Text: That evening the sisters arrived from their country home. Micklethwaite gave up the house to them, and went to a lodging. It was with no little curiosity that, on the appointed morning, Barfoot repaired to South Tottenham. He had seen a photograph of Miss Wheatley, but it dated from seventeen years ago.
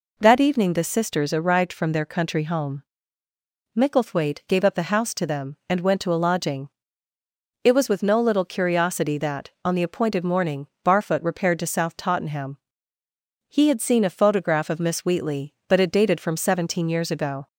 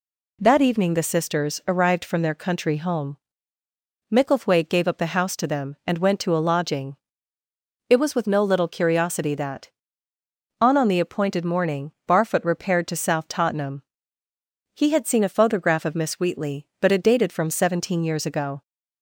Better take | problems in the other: first | says "on" twice; at 10.7 s

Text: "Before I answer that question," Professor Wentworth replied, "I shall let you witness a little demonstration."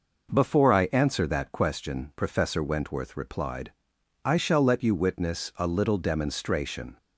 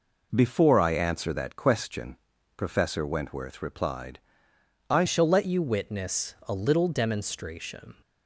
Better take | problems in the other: first | changes voice at "shall"; from 5.0 s on; 2.9 s long

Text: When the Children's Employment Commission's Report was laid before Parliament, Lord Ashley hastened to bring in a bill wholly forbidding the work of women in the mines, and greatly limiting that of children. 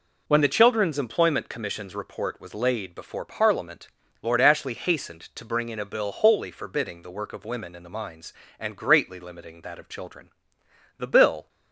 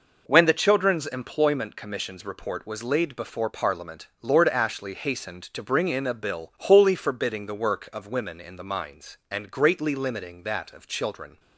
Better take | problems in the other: second | goes on to say "The bill"; from 10.9 s on; 0.52 s long

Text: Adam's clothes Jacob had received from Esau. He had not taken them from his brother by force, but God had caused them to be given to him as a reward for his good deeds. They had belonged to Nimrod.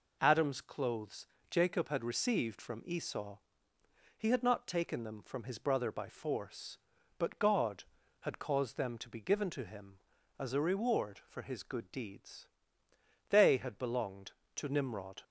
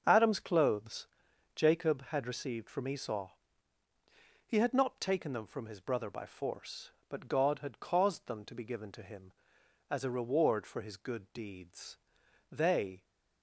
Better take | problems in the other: first | starts louder than the rest; until 1.0 s; 6.5 dB // pauses between "clothes" and "Jacob"; noticeable; at 1.0 s; 0.50 s long; slight in the first // stops before "had belonged to Nimrod"; at 13.0 s

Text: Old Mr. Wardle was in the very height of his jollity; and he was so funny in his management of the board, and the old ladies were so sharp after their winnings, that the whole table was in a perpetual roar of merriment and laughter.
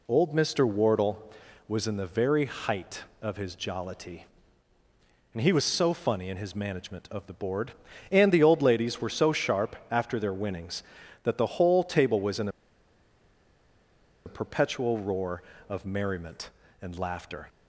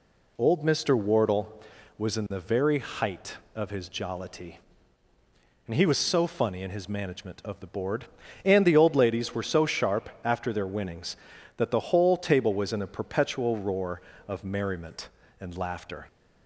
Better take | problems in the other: second | pauses between "in" and "a"; strong; at 12.4 s; 1.7 s long

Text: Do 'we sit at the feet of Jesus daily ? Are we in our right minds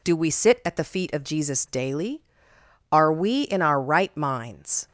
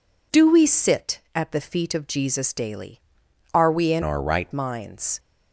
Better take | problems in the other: first | changes voice from "our" to "right"; from 4.0 to 4.5 s; 0.5 s long

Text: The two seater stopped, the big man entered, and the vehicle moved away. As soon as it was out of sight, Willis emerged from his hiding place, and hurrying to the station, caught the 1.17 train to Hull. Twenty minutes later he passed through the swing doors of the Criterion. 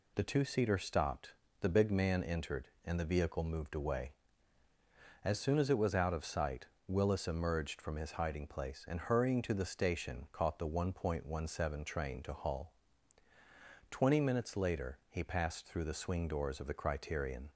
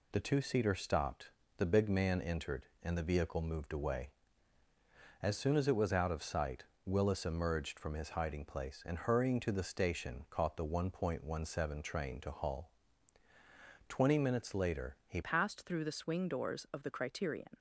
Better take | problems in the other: first | changes voice at "passed"; from 15.2 s on; 2.3 s long

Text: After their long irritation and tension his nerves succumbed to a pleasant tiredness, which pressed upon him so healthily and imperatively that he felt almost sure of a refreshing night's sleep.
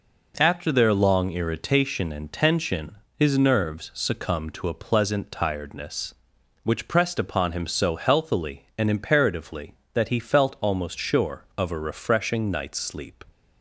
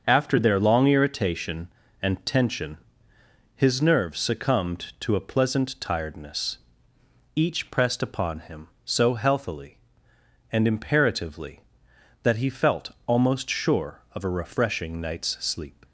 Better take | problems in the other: first | starts louder than the rest; until 1.0 s; 6.5 dB // pauses between "tension" and "his"; noticeable; at 2.7 s; 0.78 s long; slight in the first // says "each" for "which"; at 7.3 s

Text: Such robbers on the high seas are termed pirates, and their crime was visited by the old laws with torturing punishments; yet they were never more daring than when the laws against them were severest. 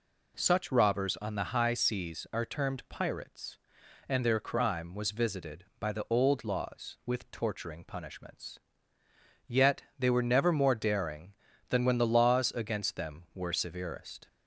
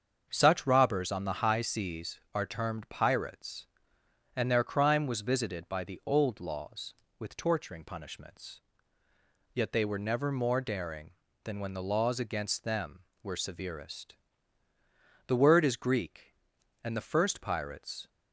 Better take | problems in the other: first | starts louder than the rest; until 1.3 s; 7 dB // goes on to say "The word is Greek and the first pirates"; strong; from 15.2 s on; 2.8 s long

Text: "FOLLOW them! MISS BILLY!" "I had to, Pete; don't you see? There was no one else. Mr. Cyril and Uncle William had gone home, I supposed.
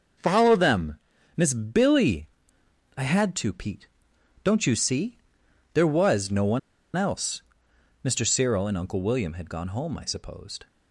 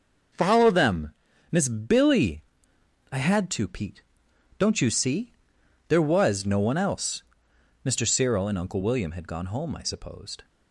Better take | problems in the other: second | starts louder than the rest; until 1.5 s; 6 dB; noticeable in the second // pauses between "one" and "else"; at 6.5 s; 0.36 s long

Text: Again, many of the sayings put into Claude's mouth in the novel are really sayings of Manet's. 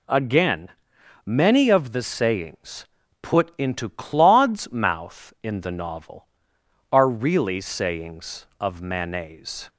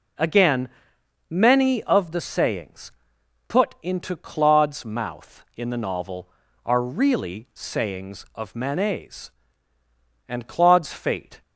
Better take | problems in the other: first | pauses between "sayings" and "put"; noticeable; at 2.9 s; 0.56 s long; slight in the first // goes on to say "And Claude's fate"; noticeable; from 10.2 s on; 1.1 s long

